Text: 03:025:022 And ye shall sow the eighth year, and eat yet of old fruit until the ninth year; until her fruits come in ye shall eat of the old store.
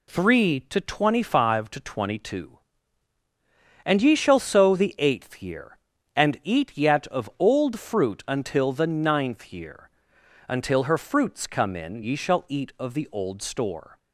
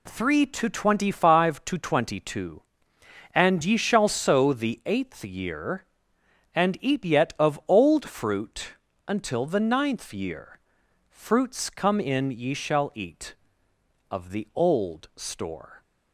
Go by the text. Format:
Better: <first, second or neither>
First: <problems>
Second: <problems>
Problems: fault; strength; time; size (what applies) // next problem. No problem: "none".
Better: first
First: none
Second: pauses between "fruit" and "until"; slight; at 8.7 s; 0.34 s long // skips "until her"; at 10.8 s